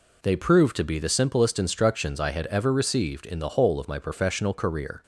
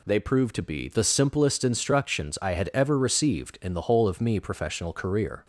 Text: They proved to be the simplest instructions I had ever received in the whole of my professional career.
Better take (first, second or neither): first